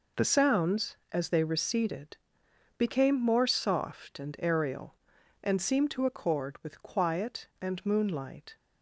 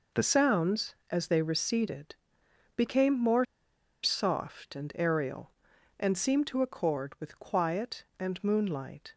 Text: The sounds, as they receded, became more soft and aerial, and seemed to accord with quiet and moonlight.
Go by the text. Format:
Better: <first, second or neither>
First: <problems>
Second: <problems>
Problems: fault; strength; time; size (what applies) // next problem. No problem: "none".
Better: first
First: none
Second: pauses between "more" and "soft"; noticeable; at 3.4 s; 0.58 s long